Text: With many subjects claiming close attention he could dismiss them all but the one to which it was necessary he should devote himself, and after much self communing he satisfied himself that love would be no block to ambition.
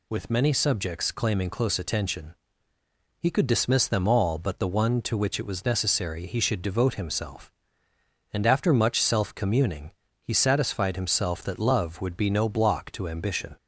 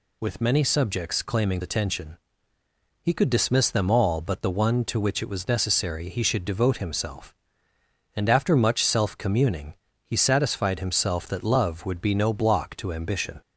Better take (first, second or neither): first